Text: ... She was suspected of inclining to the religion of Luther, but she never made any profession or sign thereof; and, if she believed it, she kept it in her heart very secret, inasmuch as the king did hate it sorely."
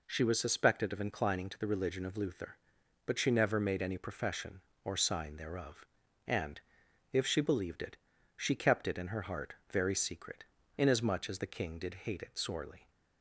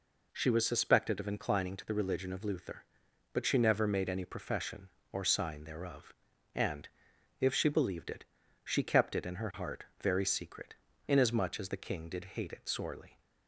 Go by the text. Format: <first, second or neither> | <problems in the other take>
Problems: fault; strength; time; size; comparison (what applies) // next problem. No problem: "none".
neither | pauses between "heart" and "very"; slight; the same in both